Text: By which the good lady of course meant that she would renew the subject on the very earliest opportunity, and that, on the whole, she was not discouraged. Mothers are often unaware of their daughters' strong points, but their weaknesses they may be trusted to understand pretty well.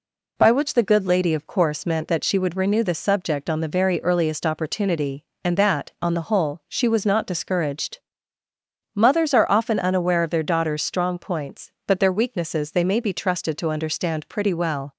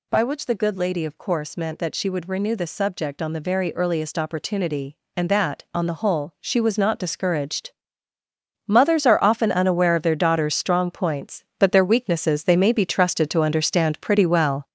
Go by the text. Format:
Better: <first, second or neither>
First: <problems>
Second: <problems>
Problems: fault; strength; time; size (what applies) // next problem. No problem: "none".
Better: first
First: none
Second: gets louder; noticeable; throughout; 5 dB